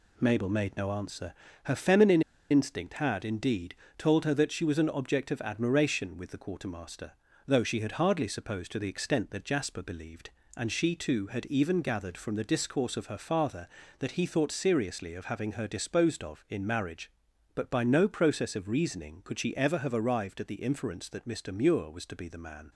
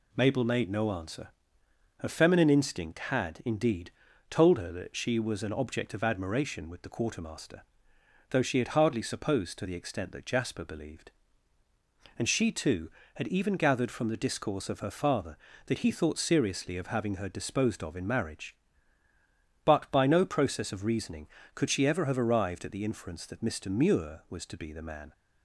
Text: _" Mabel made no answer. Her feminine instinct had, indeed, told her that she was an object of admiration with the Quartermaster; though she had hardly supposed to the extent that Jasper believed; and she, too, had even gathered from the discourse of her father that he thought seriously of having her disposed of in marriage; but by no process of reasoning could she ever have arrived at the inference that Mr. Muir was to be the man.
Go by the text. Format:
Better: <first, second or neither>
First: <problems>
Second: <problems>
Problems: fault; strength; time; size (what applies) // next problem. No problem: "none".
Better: second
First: pauses between "feminine" and "instinct"; slight; at 2.2 s; 0.28 s long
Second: none